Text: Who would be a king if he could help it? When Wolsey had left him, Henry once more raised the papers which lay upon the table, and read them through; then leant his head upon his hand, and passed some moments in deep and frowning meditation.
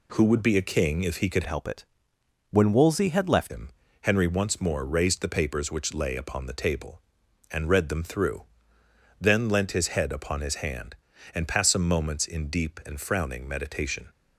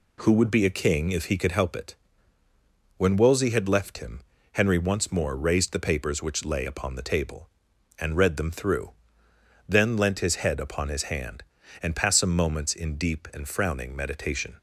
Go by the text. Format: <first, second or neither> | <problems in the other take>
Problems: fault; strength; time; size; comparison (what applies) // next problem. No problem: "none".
second | changes voice from "help" to "left"; from 1.4 to 3.5 s; 2.1 s long